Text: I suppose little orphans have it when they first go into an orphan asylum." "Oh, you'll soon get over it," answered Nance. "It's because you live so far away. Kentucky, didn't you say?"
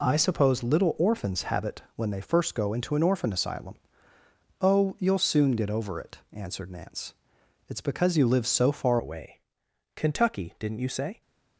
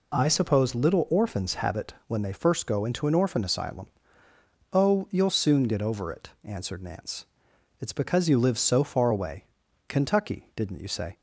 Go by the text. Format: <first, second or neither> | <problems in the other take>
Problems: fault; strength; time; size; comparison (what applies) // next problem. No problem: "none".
second | changes voice at "away"; from 8.9 s on; 2.3 s long